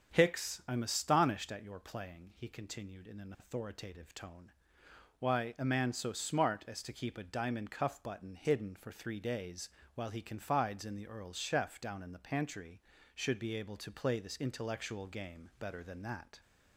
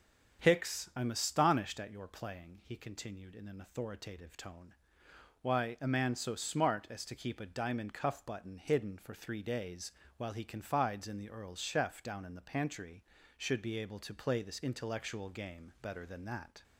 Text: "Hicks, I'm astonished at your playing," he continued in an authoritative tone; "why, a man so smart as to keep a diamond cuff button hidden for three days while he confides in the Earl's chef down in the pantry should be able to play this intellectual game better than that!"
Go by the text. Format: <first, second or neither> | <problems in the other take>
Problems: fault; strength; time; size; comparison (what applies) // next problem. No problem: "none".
neither | starts louder than the rest; strong; the same in both // pauses between "days" and "while"; slight; the same in both